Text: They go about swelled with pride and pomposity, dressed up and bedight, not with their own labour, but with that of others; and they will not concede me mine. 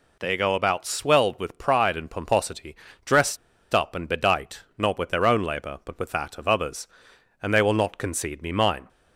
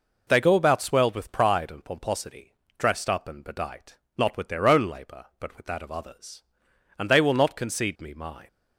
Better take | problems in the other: second | pauses between "dressed" and "up"; at 3.3 s; 0.37 s long

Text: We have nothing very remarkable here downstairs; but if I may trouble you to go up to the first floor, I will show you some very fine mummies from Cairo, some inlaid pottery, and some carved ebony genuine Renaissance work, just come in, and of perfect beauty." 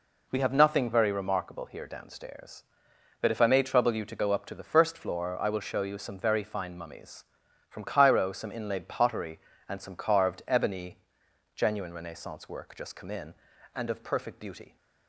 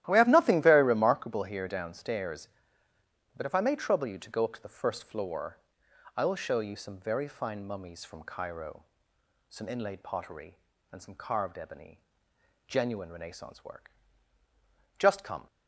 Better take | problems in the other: first | starts louder than the rest; strong; until 1.0 s; 13.5 dB // pauses between "ebony" and "genuine"; noticeable; at 12.0 s; 0.66 s long; noticeable in the first // stops before "in and of perfect beauty"; at 15.4 s

